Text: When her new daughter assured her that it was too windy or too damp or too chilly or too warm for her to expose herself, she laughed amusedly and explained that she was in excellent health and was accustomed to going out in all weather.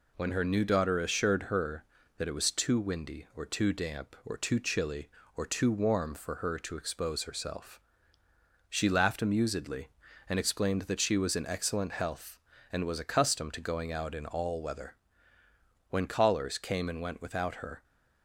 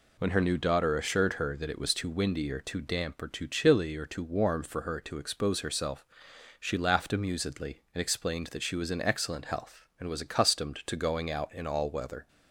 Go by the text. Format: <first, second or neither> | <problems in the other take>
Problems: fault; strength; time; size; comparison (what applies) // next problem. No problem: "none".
second | goes on to say "When callers came and went without her"; strong; from 15.8 s on; 1.9 s long